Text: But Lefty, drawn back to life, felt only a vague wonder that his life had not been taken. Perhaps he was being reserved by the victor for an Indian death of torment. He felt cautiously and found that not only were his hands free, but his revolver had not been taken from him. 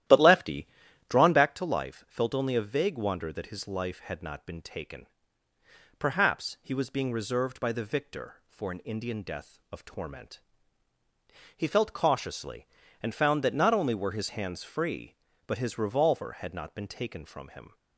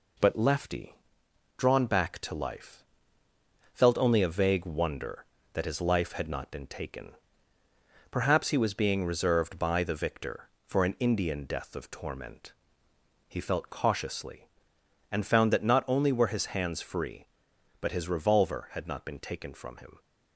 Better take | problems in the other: second | starts louder than the rest; strong; until 1.4 s; 12.5 dB

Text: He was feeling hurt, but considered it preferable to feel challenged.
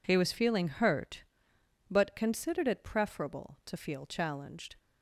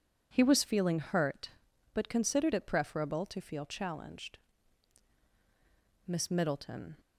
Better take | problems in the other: first | goes on to say "Miss Middleton"; noticeable; from 6.0 s on; 0.92 s long

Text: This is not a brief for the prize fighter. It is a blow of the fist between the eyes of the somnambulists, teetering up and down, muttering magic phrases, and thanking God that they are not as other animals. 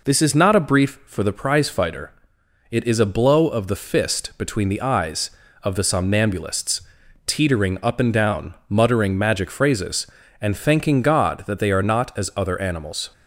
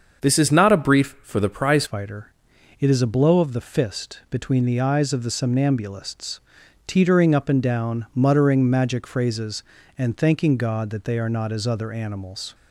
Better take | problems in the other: first | starts louder than the rest; until 1.2 s; 7 dB // changes voice at "fighter"; from 1.8 s on; 10.7 s long

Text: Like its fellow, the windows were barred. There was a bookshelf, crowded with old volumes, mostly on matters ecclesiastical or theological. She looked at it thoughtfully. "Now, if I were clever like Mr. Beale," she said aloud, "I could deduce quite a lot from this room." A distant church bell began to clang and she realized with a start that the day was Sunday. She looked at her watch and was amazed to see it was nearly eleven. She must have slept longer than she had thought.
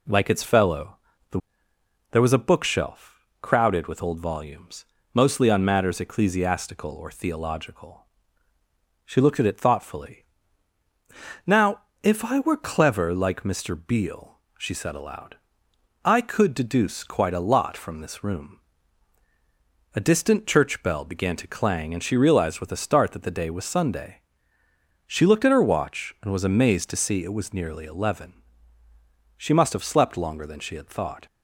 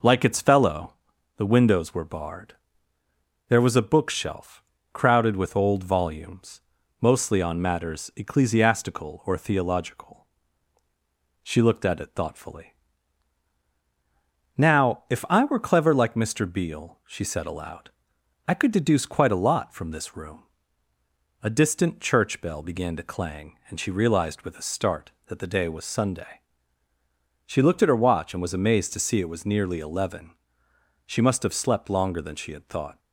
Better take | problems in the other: second | skips "windows were barred"; at 1.7 s

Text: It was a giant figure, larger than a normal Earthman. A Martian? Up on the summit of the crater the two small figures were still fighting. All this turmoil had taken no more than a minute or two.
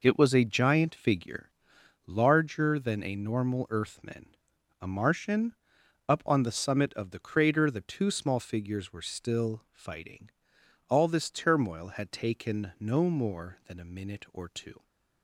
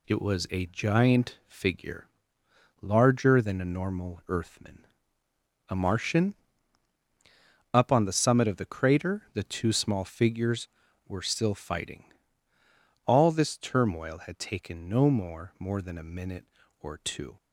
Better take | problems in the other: first | says "more" twice; at 15.5 s

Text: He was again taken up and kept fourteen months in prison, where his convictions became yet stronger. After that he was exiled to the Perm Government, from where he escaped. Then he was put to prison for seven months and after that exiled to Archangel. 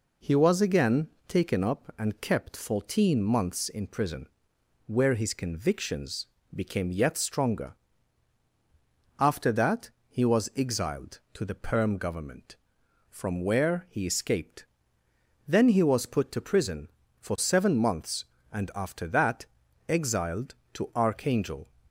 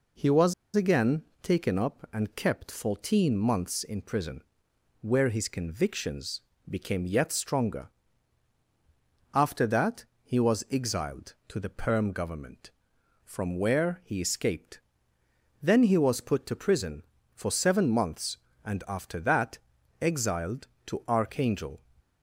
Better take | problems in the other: first | pauses between "was" and "again"; slight; at 0.5 s; 0.22 s long // pauses between "again" and "taken"; slight; at 1.2 s; 0.18 s long; slight in the first // pauses between "convictions" and "became"; slight; at 6.4 s; 0.26 s long; slight in the first // pauses between "that" and "he"; slight; at 10.0 s; 0.18 s long; slight in the first // pauses between "that" and "exiled"; noticeable; at 19.5 s; 0.46 s long; noticeable in the first

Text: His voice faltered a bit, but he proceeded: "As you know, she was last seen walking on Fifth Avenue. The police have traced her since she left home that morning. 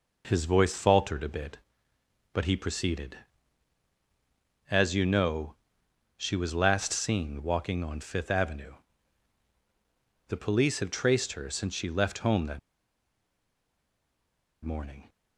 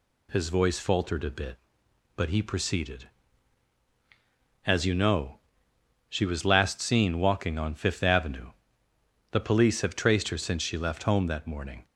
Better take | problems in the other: second | pauses between "that" and "morning"; strong; at 12.5 s; 2.0 s long

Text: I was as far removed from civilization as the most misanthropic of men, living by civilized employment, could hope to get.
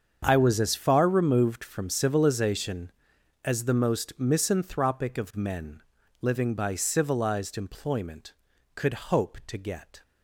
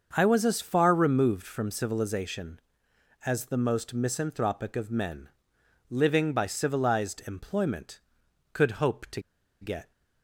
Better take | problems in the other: first | starts louder than the rest; until 1.1 s; 6.5 dB; strong in the first // pauses between "to" and "get"; at 9.2 s; 0.39 s long

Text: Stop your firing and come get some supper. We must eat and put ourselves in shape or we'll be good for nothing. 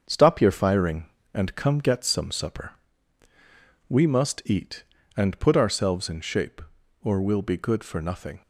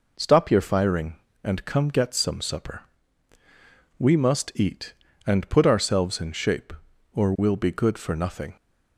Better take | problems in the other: second | gets quieter; noticeable; throughout; 6 dB

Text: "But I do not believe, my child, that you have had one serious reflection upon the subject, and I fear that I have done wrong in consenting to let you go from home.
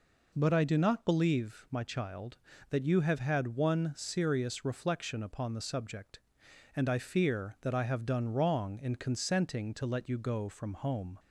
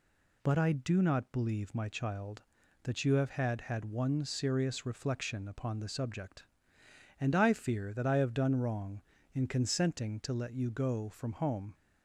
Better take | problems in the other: first | says "had" twice; at 3.5 s

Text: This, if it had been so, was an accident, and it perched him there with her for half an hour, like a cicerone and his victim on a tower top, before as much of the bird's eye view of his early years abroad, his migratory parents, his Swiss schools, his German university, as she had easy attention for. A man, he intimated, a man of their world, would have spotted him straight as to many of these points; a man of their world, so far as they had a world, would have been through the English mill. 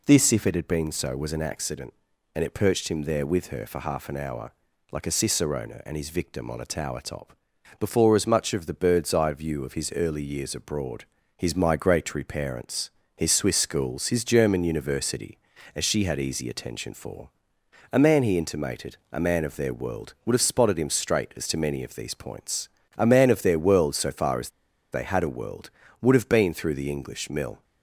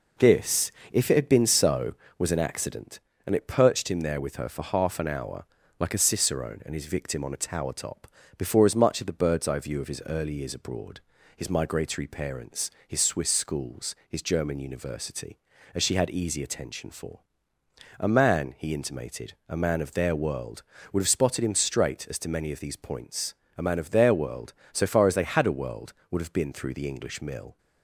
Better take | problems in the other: second | pauses between "as" and "they"; at 24.4 s; 0.42 s long

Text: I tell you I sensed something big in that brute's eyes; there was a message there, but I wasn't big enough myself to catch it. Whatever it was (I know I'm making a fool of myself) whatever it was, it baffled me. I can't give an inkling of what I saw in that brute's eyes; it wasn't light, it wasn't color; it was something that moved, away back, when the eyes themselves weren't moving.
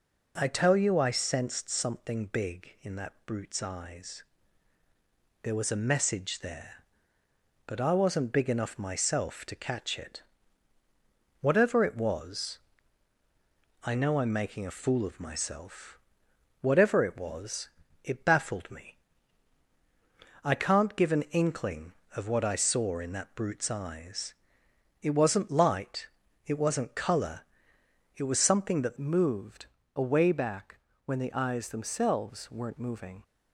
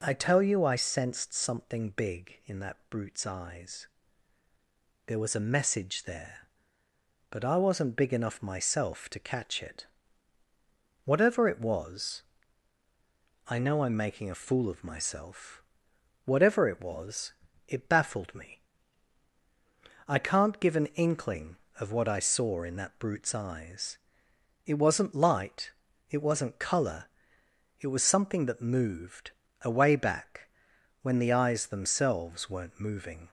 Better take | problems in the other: second | changes voice at "moved"; from 28.9 s on; 4.3 s long

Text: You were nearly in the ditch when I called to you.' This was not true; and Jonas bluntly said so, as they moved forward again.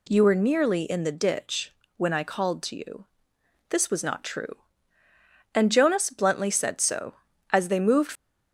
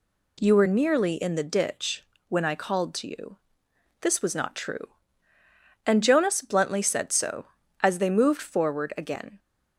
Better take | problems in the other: second | pauses between "ditch" and "when"; slight; at 1.7 s; 0.24 s long; slight in the second // stops before "forward again"; at 8.1 s

